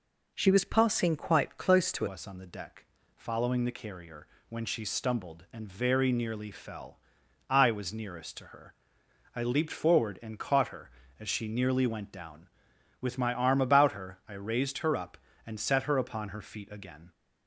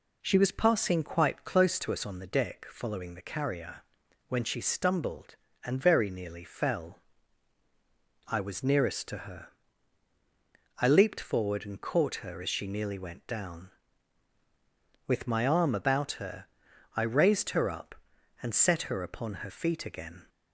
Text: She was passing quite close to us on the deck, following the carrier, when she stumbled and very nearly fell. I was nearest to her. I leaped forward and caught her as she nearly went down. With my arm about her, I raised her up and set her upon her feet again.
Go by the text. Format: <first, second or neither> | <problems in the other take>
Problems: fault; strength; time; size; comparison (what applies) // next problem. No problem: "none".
second | changes voice at "us"; from 2.0 s on; 15.1 s long